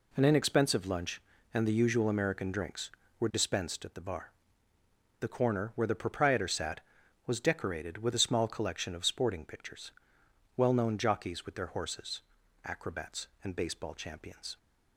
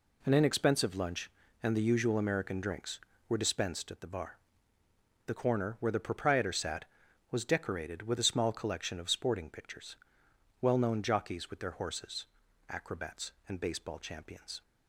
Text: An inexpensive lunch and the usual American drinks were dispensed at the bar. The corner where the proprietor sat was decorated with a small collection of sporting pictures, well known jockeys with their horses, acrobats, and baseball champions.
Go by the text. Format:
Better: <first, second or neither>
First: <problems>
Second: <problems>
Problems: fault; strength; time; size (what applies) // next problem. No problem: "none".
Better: neither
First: none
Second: none